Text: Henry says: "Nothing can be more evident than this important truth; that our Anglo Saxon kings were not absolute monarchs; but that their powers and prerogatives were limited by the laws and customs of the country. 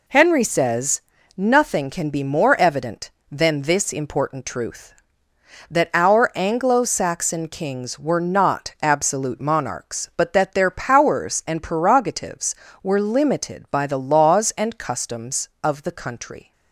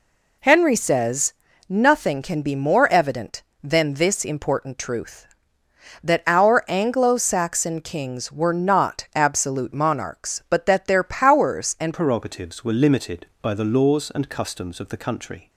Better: first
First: none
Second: changes voice at "prerogatives"; from 11.9 s on; 3.5 s long

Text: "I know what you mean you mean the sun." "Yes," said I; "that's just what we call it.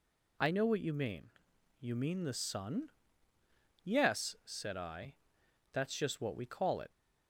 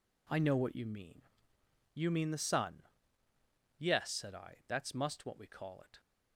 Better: first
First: pauses between "mean" and "you"; noticeable; at 1.3 s; 0.48 s long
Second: pauses between "mean" and "you"; noticeable; at 1.2 s; 0.72 s long // says "must" for "just"; at 4.9 s

